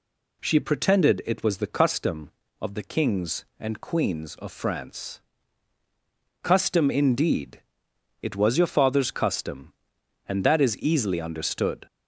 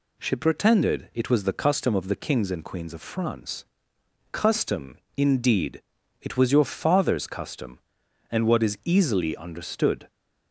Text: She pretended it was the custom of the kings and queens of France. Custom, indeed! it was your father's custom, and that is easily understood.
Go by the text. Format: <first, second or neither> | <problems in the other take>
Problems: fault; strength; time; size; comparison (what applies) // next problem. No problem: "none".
first | says "what" for "that"; at 8.4 s